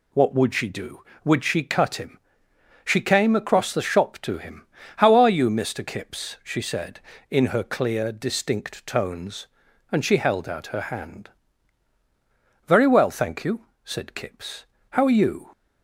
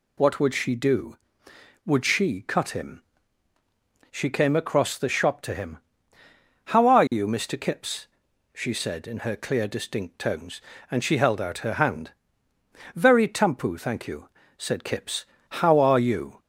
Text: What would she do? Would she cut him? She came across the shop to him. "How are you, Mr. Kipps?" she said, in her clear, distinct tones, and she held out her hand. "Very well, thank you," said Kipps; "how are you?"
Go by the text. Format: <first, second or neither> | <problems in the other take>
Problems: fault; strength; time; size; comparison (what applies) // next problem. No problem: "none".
first | says "tampu" for "well"; at 13.2 s